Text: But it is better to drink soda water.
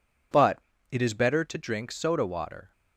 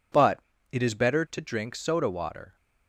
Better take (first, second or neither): neither